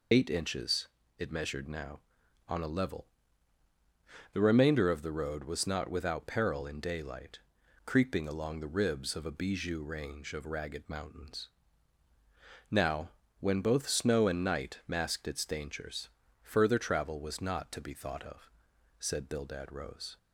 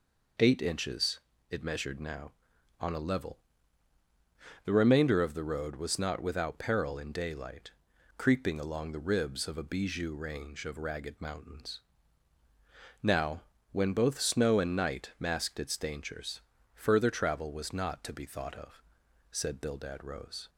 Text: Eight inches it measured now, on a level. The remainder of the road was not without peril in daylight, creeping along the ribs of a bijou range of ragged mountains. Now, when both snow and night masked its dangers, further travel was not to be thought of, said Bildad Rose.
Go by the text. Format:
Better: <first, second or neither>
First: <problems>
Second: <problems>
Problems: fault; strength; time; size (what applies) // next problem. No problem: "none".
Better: second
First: loses the start of "Eight"; at 0.1 s; 40 ms // pauses between "inches" and "it"; slight; at 0.8 s; 0.30 s long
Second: pauses between "inches" and "it"; slight; at 1.1 s; 0.30 s long